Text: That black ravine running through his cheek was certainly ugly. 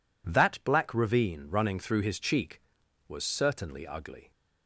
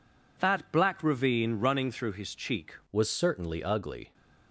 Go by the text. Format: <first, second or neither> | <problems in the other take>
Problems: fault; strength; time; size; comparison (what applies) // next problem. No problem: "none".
first | changes voice at "was"; from 2.9 s on; 1.2 s long